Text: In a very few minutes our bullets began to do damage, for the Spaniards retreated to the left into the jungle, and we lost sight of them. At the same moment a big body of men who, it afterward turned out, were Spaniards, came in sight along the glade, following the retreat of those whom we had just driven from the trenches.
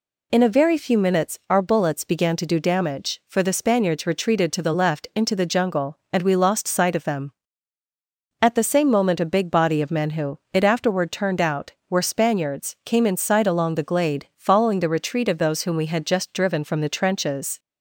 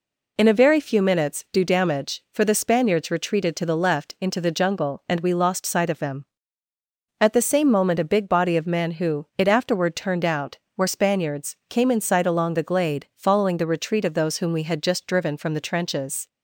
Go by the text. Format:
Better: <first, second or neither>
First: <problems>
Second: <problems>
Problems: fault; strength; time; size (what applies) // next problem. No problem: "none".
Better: first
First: none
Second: skips "our bullets began to"; at 1.4 s